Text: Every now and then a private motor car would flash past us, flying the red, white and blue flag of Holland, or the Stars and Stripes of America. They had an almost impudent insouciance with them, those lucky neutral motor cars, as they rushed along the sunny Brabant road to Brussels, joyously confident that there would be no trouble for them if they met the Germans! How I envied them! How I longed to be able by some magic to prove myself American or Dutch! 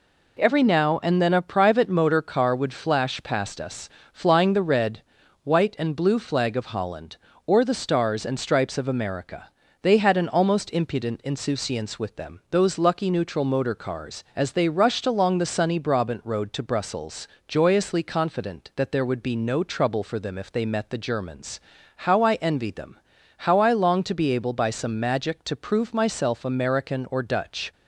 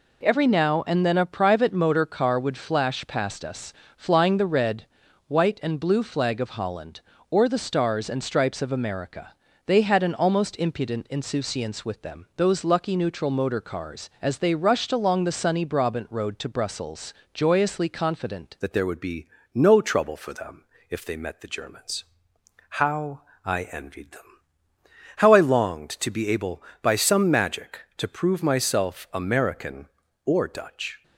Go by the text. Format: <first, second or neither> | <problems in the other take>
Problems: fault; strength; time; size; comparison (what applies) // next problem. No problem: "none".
first | changes voice at "that"; from 18.6 s on; 12.4 s long // pauses between "be" and "no"; slight; at 19.2 s; 0.26 s long // pauses between "them" and "if"; slight; at 20.6 s; 0.24 s long // pauses between "How" and "I"; slight; at 23.2 s; 0.22 s long